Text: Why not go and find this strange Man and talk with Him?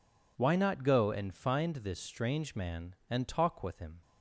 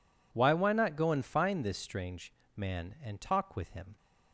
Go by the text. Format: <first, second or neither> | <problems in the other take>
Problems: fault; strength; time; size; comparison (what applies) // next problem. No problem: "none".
first | says "Why" twice; at 0.5 s // pauses between "strange" and "Man"; slight; at 2.3 s; 0.24 s long